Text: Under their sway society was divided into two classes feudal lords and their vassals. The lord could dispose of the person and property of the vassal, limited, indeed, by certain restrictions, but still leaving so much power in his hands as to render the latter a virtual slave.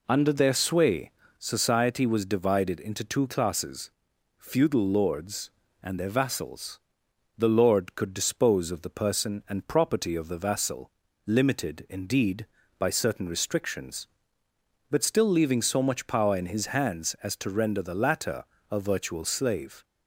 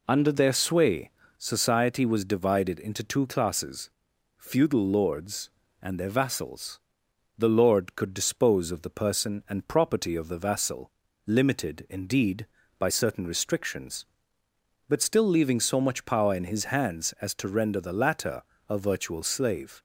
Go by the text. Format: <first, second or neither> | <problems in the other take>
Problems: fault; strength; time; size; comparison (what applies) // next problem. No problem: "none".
neither | pauses between "sway" and "society"; slight; the same in both // pauses between "classes" and "feudal"; noticeable; the same in both // pauses between "latter" and "a"; slight; the same in both